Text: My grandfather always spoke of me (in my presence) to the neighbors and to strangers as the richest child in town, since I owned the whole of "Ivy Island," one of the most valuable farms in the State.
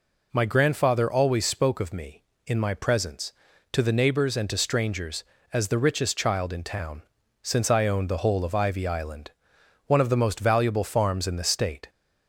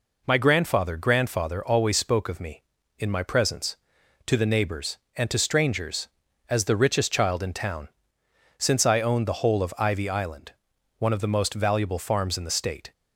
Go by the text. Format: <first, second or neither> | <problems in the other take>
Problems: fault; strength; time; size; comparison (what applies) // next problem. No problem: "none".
first | says "grandfather" twice; at 0.9 s